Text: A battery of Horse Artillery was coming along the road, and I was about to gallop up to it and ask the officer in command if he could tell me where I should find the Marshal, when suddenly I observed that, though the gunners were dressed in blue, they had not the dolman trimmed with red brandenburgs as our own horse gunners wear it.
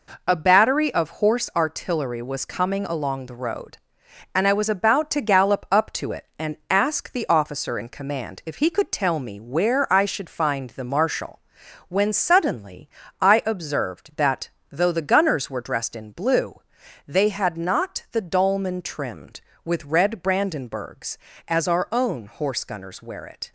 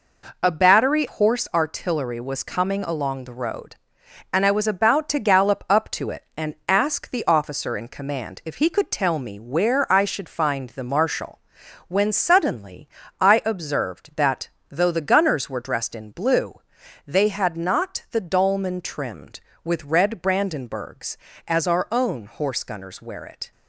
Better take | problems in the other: first | skips "of"; at 1.0 s // pauses between "suddenly" and "I"; slight; at 12.8 s; 0.32 s long; slight in the first

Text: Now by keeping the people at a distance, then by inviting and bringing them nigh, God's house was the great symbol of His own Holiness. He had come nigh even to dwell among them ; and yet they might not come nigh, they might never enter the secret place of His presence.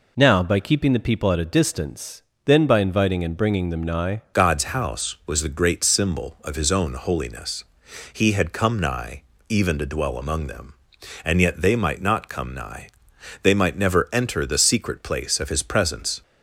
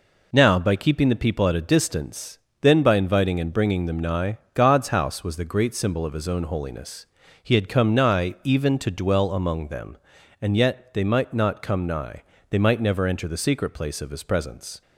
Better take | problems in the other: second | changes voice at "God's"; from 4.3 s on; 11.9 s long // pauses between "nigh" and "even"; slight; at 9.2 s; 0.26 s long

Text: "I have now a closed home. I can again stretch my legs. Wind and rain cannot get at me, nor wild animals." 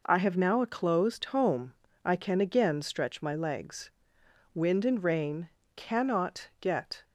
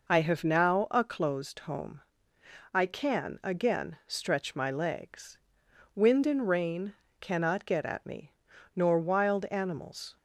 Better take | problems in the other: second | pauses between "rain" and "cannot"; slight; at 5.4 s; 0.28 s long; slight in the second // stops before "at me nor wild animals"; at 7.0 s

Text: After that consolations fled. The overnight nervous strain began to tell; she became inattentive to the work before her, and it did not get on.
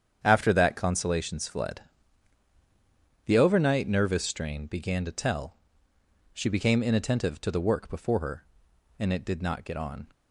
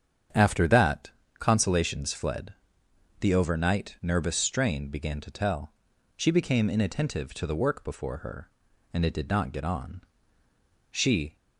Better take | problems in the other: first | starts louder than the rest; strong; until 1.6 s; 8 dB; strong in the first // pauses between "that" and "consolations"; slight; at 1.1 s; 0.28 s long // goes on to say "She"; slight; from 10.8 s on; 0.46 s long

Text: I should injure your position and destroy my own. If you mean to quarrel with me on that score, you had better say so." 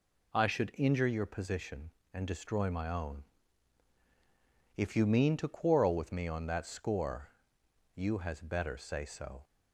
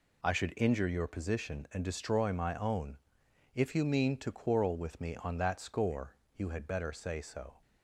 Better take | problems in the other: second | says "has" for "had"; at 8.1 s

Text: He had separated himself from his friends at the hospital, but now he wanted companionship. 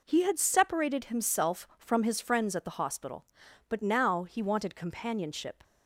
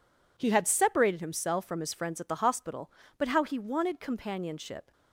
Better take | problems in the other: first | says "how" for "now"; at 3.2 s

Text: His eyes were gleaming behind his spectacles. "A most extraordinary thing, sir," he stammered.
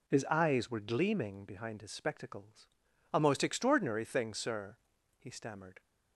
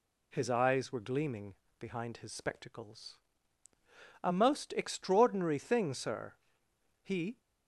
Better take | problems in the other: first | pauses between "gleaming" and "behind"; slight; at 1.5 s; 0.24 s long // stops before "stammered"; at 7.3 s

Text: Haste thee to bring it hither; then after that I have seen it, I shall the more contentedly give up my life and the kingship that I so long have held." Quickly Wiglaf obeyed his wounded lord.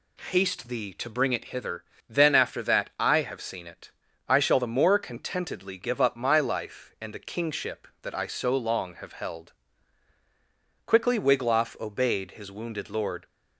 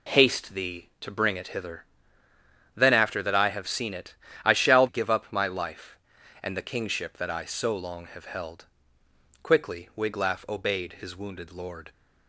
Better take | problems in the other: first | skips "the more contentedly"; at 4.8 s

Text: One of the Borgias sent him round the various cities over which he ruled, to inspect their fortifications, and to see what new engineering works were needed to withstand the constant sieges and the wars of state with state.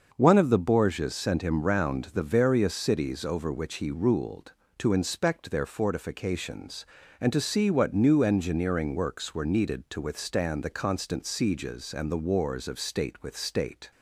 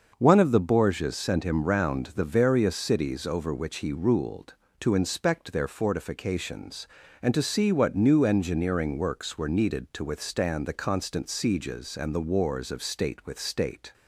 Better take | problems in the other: neither | starts louder than the rest; the same in both

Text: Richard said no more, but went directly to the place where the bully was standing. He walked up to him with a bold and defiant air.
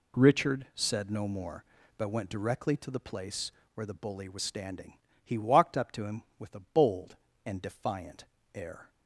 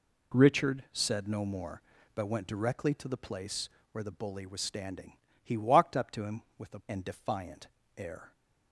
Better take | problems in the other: first | pauses between "place" and "where"; slight; at 3.6 s; 0.24 s long; slight in the first // skips "bold"; at 6.8 s // pauses between "defiant" and "air"; slight; at 7.6 s; 0.28 s long; slight in the first

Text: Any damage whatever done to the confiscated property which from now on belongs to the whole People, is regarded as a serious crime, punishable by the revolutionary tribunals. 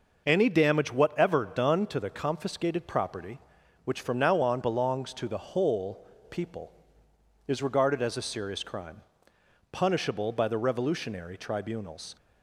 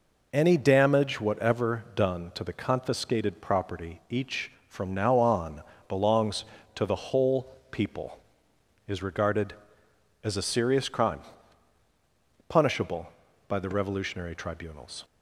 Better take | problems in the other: first | says "each" for "which"; at 4.0 s // pauses between "on" and "belongs"; slight; at 5.6 s; 0.28 s long // pauses between "whole" and "People"; slight; at 7.5 s; 0.20 s long; slight in the first

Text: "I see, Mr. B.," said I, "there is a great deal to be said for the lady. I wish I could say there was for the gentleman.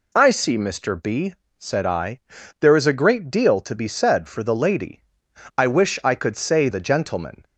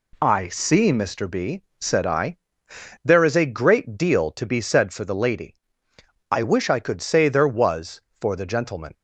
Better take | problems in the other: second | skips "there was for"; at 6.6 s

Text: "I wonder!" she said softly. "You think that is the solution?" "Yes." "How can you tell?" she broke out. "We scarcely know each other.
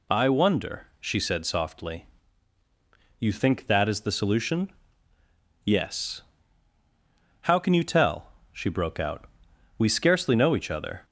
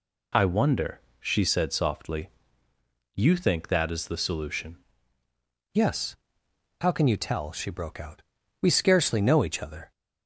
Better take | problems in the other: first | changes voice at "Yes"; from 5.7 s on; 4.2 s long

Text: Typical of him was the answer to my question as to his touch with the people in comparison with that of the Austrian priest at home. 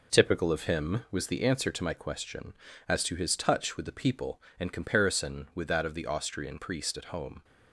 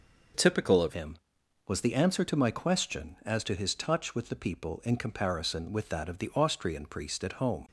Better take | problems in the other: first | changes voice at "him"; from 0.9 s on; 6.7 s long

